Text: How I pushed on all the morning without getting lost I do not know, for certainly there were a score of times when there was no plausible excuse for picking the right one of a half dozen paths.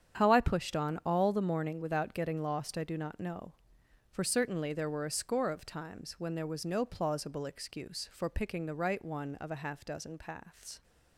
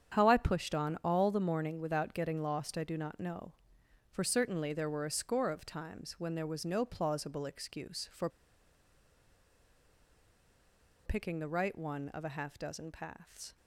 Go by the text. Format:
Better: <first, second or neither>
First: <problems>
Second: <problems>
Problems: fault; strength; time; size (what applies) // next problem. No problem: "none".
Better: first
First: starts louder than the rest; strong; until 1.2 s; 8.5 dB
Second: starts louder than the rest; strong; until 1.1 s; 8.5 dB // pauses between "for" and "picking"; strong; at 8.2 s; 2.7 s long